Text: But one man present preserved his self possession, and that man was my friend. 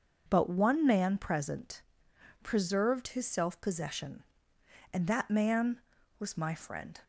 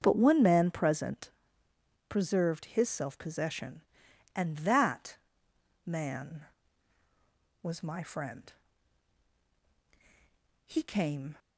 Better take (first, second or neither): first